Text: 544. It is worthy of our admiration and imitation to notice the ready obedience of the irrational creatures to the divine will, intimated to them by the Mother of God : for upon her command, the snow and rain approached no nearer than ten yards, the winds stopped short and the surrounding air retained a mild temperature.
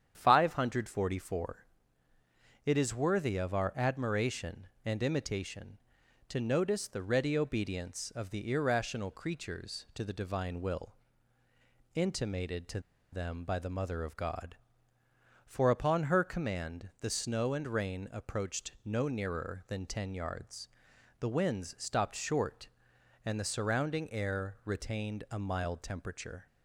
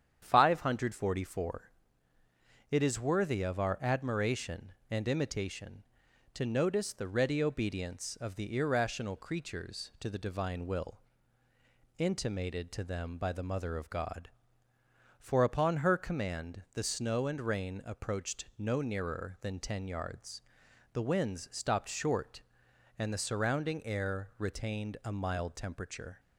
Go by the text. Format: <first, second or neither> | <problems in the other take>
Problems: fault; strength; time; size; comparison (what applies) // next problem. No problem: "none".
second | starts louder than the rest; strong; until 1.1 s; 9 dB; strong in the second // pauses between "to" and "them"; slight; at 12.7 s; 0.32 s long